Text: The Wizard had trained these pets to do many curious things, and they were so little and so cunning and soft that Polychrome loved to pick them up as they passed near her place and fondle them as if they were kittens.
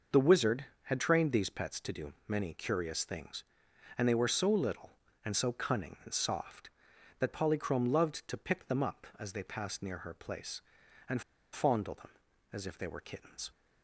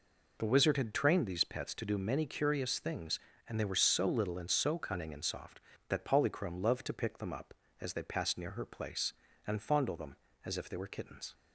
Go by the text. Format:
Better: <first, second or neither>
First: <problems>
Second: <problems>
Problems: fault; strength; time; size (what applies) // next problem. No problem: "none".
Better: second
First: pauses between "do" and "many"; slight; at 2.1 s; 0.16 s long // pauses between "and" and "fondle"; slight; at 11.2 s; 0.31 s long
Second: none